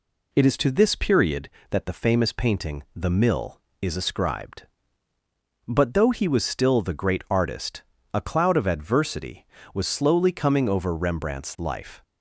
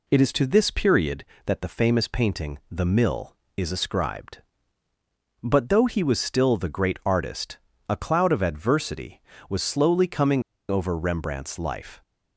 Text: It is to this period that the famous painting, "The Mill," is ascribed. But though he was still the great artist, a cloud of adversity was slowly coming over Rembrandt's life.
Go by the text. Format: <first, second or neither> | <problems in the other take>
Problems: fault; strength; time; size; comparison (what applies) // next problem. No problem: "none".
first | pauses between "coming" and "over"; slight; at 10.4 s; 0.29 s long